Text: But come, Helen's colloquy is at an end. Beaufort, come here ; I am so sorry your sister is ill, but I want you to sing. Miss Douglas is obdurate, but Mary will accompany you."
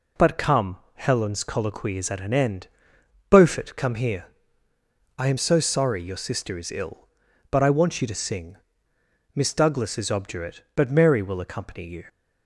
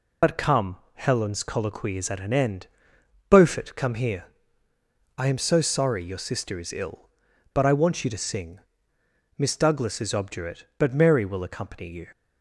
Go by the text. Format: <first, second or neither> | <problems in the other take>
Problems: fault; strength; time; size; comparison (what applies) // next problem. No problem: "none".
first | loses the start of "But"; at 0.2 s; 65 ms